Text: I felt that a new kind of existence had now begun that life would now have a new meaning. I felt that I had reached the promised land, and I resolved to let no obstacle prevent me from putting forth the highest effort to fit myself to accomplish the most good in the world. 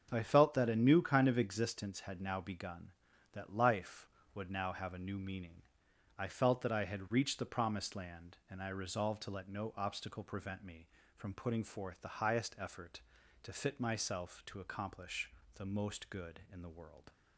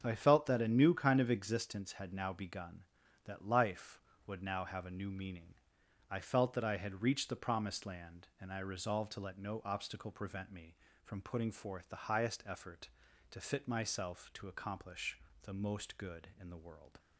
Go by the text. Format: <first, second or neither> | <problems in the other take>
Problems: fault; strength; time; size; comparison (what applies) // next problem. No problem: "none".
neither | starts louder than the rest; the same in both // pauses between "accomplish" and "the"; slight; the same in both